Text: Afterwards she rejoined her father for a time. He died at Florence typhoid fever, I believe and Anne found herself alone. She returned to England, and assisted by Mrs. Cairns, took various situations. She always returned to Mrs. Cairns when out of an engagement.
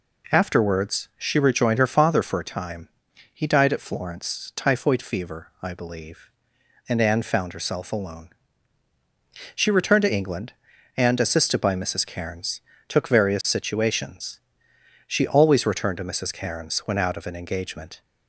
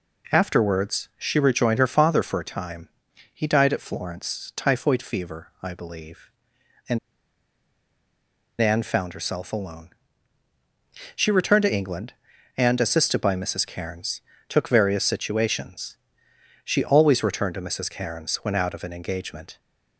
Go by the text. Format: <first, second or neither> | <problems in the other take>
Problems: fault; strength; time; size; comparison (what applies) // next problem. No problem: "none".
first | pauses between "and" and "Anne"; strong; at 6.9 s; 1.6 s long